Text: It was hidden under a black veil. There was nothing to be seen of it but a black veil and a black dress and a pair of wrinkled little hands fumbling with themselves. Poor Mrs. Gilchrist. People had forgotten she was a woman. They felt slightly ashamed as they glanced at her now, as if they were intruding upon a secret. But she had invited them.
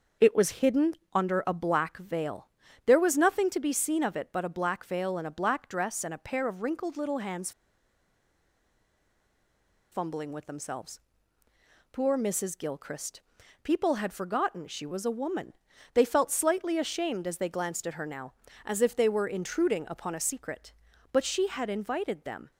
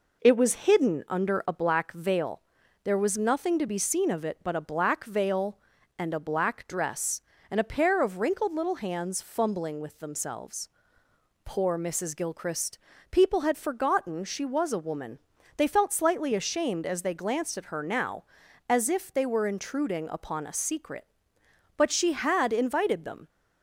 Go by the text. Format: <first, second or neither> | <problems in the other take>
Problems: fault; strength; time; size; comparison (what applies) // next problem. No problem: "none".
second | starts louder than the rest; until 1.3 s; 6 dB // pauses between "hidden" and "under"; slight; at 0.9 s; 0.18 s long // pauses between "hands" and "fumbling"; strong; at 7.5 s; 2.4 s long